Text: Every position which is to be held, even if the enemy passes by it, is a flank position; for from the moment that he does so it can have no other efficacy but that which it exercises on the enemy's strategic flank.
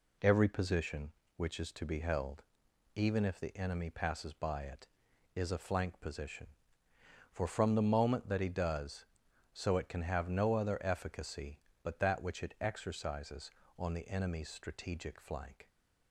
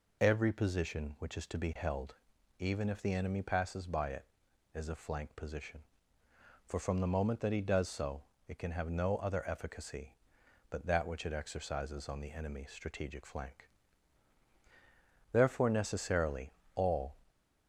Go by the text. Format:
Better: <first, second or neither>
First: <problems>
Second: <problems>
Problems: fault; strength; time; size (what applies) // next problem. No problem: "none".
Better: first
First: none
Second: pauses between "so" and "it"; slight; at 8.2 s; 0.26 s long // goes on to say "Therefore necessarily all"; strong; from 15.3 s on; 1.8 s long